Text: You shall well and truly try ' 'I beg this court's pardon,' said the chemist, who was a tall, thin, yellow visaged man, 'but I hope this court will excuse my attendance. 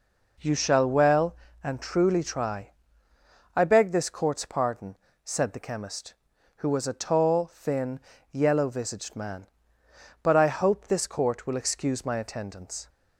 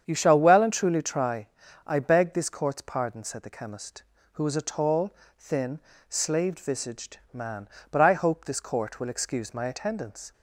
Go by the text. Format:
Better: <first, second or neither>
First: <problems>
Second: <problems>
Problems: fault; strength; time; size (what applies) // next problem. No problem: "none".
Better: first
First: none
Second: starts louder than the rest; strong; until 1.0 s; 8 dB // says "slaved" for "yellow"; at 6.0 s // pauses between "visaged" and "man"; slight; at 7.1 s; 0.16 s long